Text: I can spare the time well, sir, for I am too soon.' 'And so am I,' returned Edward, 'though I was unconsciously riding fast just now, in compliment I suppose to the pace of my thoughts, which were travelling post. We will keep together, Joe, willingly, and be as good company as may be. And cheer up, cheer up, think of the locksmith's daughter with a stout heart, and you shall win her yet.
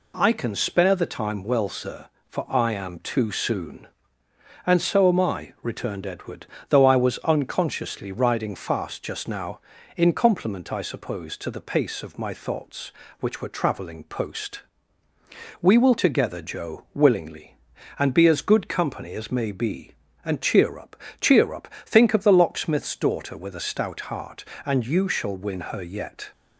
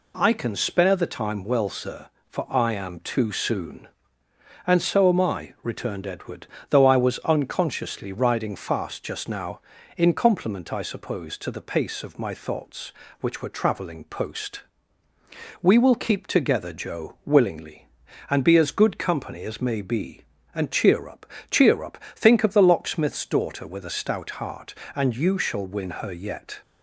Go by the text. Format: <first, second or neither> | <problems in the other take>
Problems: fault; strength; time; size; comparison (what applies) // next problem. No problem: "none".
second | skips "keep"; at 15.9 s